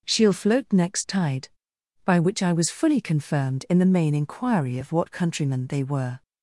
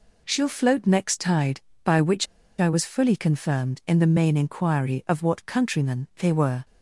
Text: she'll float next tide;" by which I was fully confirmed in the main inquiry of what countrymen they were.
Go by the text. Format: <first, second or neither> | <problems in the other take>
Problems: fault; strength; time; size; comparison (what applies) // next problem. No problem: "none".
first | pauses between "which" and "I"; slight; at 2.2 s; 0.33 s long